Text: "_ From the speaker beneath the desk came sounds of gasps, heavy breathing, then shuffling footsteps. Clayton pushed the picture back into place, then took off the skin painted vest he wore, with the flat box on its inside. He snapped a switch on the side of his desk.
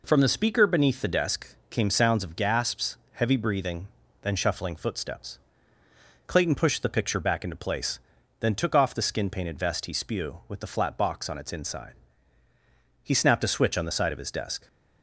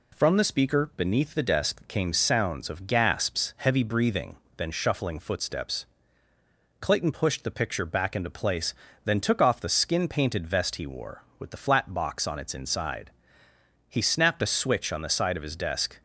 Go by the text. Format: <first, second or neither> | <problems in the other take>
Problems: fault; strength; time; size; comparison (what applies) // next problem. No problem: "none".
second | pauses between "desk" and "came"; slight; at 1.5 s; 0.16 s long // says "spew" for "wore"; at 9.9 s